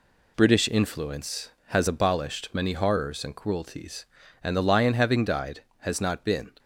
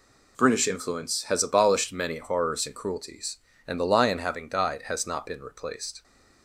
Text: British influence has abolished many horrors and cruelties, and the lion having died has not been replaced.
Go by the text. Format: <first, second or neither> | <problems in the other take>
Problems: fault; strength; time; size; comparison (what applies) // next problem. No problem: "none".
second | stops before "replaced"; at 6.5 s